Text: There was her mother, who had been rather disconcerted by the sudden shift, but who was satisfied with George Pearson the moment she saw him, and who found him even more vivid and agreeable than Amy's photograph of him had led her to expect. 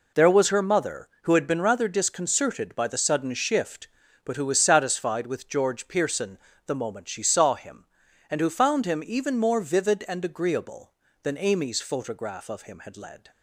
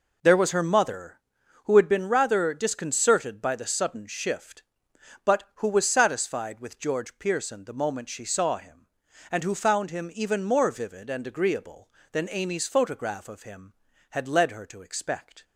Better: second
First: pauses between "Pearson" and "the"; slight; at 6.3 s; 0.30 s long // stops before "her to expect"; at 13.3 s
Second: none

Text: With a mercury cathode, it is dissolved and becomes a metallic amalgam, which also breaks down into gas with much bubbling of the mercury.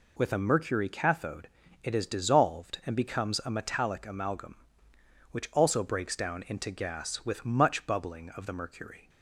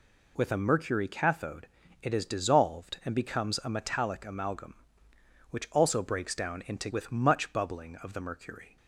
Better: first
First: none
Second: skips "gas"; at 6.9 s

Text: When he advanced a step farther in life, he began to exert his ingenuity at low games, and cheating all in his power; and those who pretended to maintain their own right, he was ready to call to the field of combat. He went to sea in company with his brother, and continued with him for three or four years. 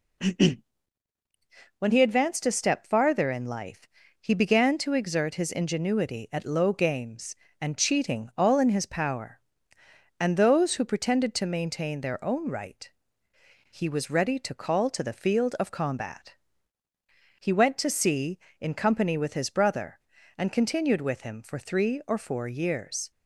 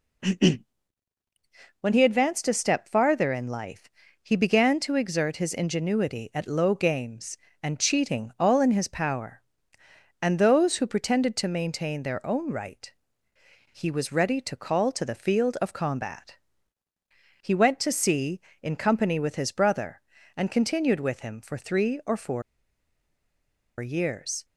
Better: first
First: none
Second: pauses between "four" and "years"; strong; at 22.4 s; 1.3 s long

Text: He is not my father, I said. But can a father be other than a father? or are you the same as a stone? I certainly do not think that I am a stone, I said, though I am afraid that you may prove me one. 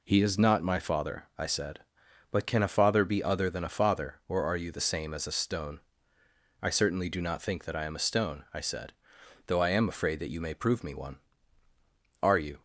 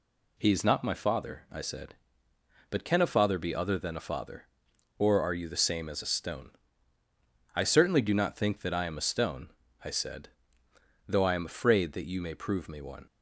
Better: second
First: goes on to say "Are you"; slight; from 12.2 s on; 0.40 s long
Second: none

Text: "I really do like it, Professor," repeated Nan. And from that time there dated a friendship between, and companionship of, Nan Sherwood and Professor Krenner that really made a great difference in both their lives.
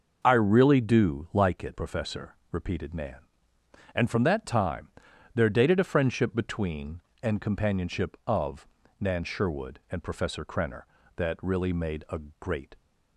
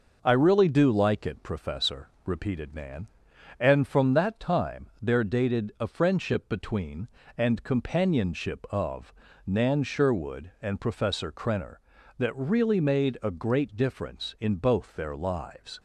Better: second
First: pauses between "time" and "there"; at 4.8 s; 0.44 s long // pauses between "a" and "great"; slight; at 12.1 s; 0.18 s long // stops before "difference in both their lives"; at 12.7 s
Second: none

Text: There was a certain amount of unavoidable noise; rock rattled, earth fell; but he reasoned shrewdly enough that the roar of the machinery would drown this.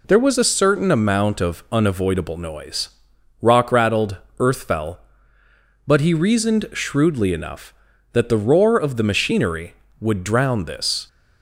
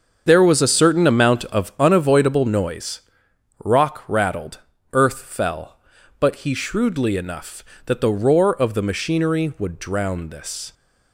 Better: first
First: none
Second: starts louder than the rest; until 1.2 s; 7 dB // skips "reasoned"; at 6.5 s

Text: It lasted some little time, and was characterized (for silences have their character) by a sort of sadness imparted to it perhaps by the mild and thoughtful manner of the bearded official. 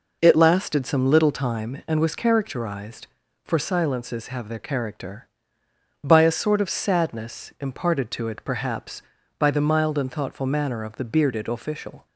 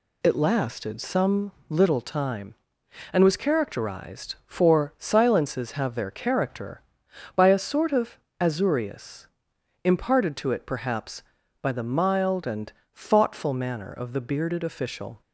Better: first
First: none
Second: pauses between "some" and "little"; slight; at 1.5 s; 0.18 s long // says "azureus" for "sadness"; at 8.3 s // pauses between "and" and "thoughtful"; slight; at 12.7 s; 0.24 s long

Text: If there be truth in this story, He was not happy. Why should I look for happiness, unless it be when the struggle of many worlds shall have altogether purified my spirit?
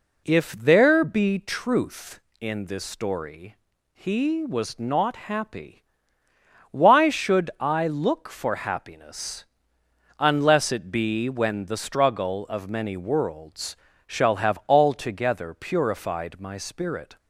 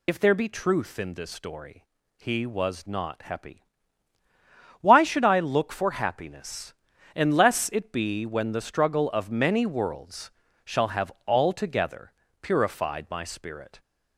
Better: first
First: pauses between "worlds" and "shall"; slight; at 13.7 s; 0.30 s long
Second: loses the start of "If"; at 0.0 s; 70 ms // pauses between "worlds" and "shall"; slight; at 10.3 s; 0.34 s long // pauses between "have" and "altogether"; slight; at 11.1 s; 0.16 s long // pauses between "altogether" and "purified"; slight; at 12.1 s; 0.28 s long

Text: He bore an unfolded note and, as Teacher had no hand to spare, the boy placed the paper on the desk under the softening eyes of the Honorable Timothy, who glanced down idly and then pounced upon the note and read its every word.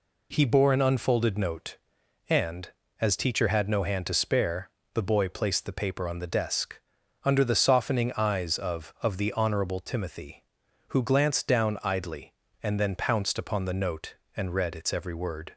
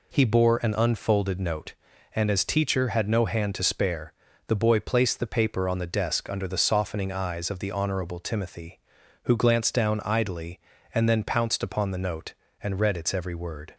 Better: second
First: pauses between "desk" and "under"; noticeable; at 6.7 s; 0.46 s long // says "of" twice; at 9.0 s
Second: none

